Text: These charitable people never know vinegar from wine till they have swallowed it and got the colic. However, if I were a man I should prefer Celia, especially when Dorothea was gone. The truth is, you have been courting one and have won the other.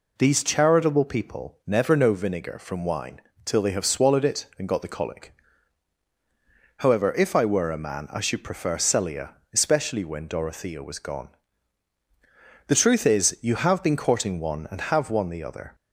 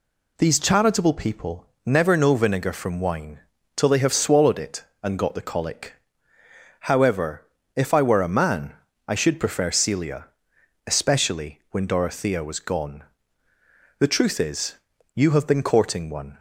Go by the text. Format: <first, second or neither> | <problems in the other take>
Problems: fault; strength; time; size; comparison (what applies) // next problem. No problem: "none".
first | pauses between "people" and "never"; slight; at 1.6 s; 0.20 s long // pauses between "wine" and "till"; slight; at 3.3 s; 0.34 s long; slight in the first // pauses between "man" and "I"; slight; at 8.7 s; 0.34 s long // stops before "and have won the other"; at 16.3 s